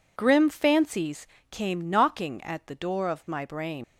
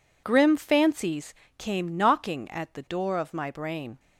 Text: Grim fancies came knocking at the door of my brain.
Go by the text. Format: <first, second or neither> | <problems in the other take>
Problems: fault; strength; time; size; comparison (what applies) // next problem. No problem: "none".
second | pauses between "fancies" and "came"; slight; at 1.2 s; 0.24 s long; slight in the second // leaves "brain" unfinished; at 3.8 s; 95 ms